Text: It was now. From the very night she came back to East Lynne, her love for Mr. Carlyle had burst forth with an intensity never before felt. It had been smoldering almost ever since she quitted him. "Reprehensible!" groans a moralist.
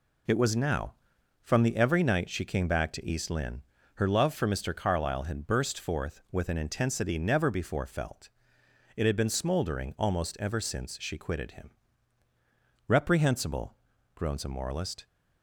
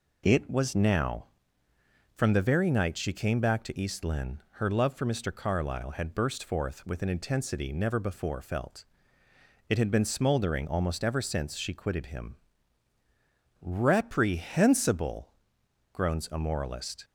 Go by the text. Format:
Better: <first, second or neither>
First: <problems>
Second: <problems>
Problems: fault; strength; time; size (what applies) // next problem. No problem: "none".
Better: second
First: says "every" for "very"; at 1.7 s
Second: none